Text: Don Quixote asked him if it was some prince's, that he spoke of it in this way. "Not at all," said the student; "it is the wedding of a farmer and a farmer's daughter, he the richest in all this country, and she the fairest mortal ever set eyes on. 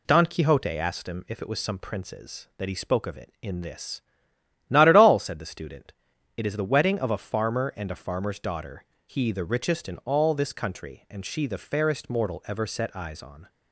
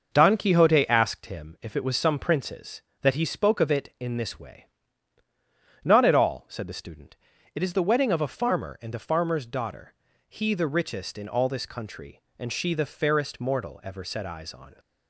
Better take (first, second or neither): second